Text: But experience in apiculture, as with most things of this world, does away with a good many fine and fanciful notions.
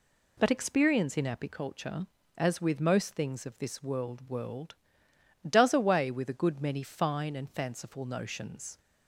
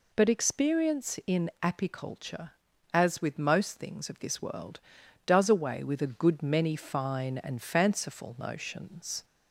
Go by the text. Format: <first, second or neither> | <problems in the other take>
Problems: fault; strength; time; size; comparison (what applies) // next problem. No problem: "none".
second | says "world" twice; at 4.2 s